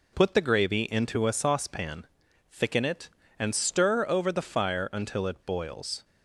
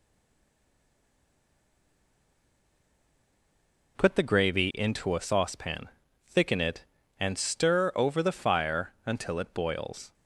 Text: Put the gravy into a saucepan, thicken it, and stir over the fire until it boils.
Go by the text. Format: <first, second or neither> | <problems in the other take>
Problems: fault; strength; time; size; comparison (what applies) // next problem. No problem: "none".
first | stays silent before the first word; strong; until 3.9 s; 3.9 s long